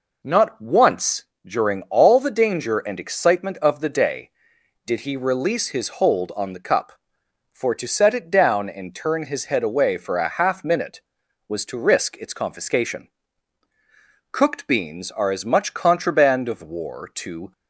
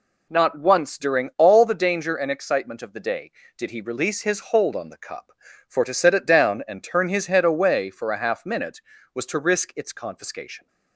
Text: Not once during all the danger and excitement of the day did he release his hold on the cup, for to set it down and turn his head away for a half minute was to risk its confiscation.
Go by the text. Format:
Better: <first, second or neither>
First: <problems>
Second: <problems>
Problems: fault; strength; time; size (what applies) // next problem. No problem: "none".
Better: second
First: pauses between "once" and "during"; slight; at 1.2 s; 0.20 s long // goes on to say "Cooked beans are as much contraband of war to"; strong; from 14.2 s on; 3.2 s long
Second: none